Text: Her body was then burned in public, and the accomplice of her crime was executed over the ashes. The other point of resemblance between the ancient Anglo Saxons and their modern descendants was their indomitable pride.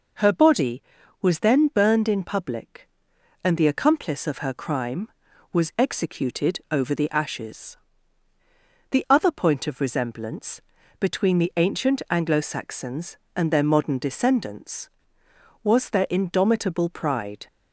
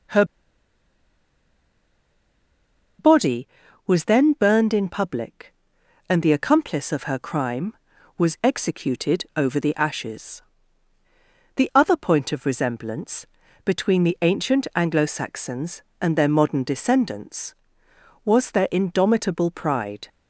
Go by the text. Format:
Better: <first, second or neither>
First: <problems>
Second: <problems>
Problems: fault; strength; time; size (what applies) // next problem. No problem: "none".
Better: first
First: pauses between "resemblance" and "between"; at 10.6 s; 0.40 s long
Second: pauses between "Her" and "body"; strong; at 0.2 s; 2.7 s long // pauses between "resemblance" and "between"; at 13.2 s; 0.40 s long